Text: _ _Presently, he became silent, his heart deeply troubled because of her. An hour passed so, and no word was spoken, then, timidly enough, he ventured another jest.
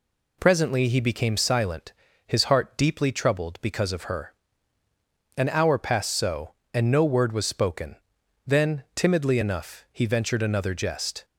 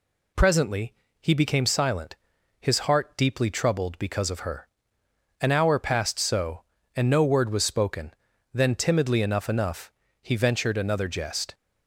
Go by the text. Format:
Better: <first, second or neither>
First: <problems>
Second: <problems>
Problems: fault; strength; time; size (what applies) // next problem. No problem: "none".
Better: first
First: none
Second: says "enough" twice; at 9.4 s